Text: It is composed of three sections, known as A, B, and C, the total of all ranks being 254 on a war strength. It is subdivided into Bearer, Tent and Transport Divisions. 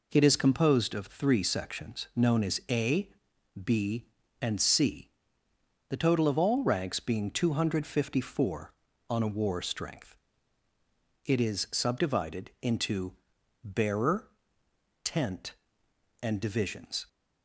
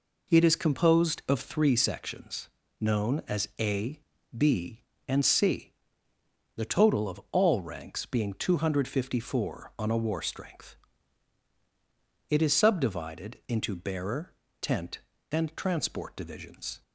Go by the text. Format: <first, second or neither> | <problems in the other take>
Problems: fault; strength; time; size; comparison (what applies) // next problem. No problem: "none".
second | pauses between "into" and "Bearer"; noticeable; at 13.1 s; 0.50 s long // skips "Transport"; at 16.3 s